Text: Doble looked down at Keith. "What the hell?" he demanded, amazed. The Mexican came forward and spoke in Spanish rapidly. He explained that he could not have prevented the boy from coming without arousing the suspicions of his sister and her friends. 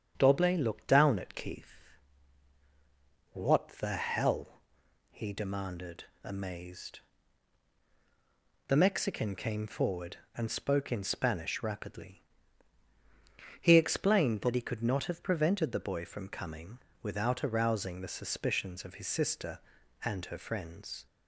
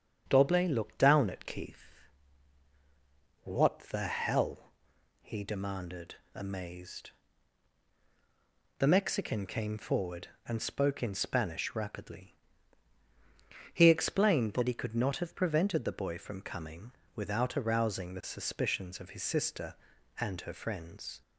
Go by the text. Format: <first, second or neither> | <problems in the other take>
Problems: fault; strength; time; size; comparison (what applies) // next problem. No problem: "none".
neither | starts louder than the rest; strong; the same in both // pauses between "coming" and "without"; slight; the same in both